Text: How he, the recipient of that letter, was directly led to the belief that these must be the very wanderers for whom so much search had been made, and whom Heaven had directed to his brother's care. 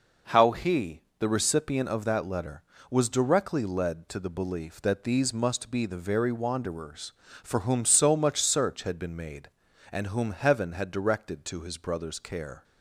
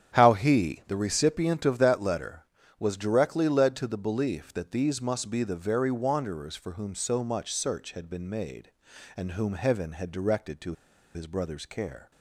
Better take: first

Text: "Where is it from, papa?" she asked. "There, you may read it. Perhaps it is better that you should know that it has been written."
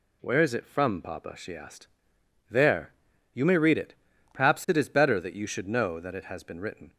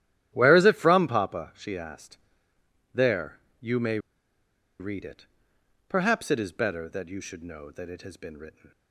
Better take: first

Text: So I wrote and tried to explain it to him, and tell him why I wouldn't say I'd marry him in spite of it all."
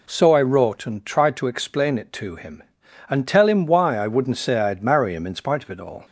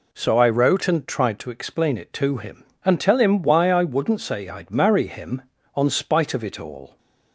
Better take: first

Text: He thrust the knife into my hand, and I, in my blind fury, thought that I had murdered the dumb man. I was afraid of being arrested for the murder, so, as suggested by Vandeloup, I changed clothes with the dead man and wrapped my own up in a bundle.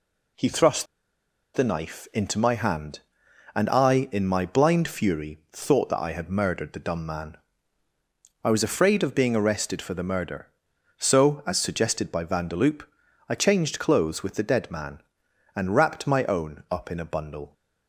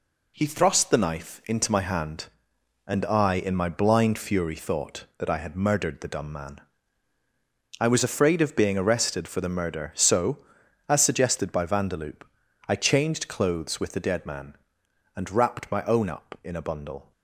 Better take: second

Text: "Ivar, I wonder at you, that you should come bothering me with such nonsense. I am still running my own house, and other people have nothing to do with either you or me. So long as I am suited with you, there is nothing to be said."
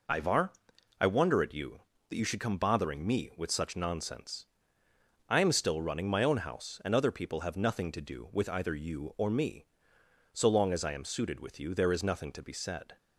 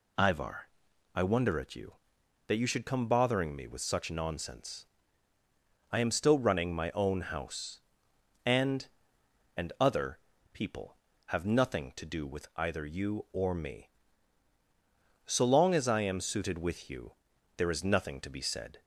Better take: first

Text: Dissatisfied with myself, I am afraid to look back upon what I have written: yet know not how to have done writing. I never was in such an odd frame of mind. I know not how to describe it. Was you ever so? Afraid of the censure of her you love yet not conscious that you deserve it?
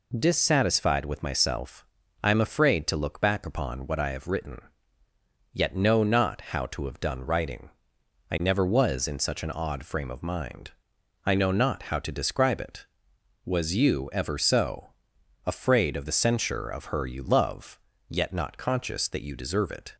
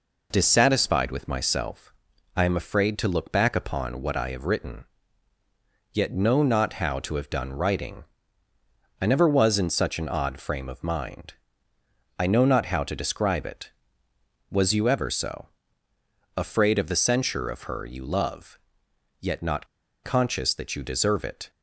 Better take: first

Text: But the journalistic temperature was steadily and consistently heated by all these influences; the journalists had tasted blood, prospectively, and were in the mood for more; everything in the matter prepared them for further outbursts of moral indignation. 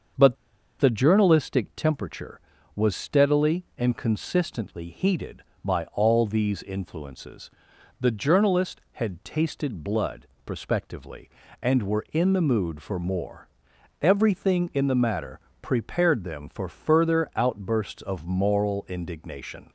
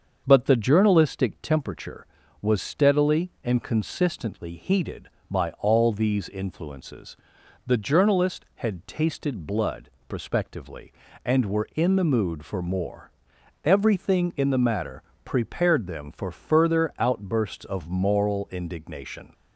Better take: second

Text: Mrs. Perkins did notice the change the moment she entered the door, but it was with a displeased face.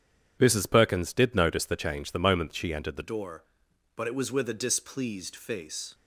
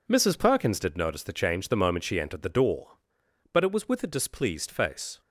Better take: second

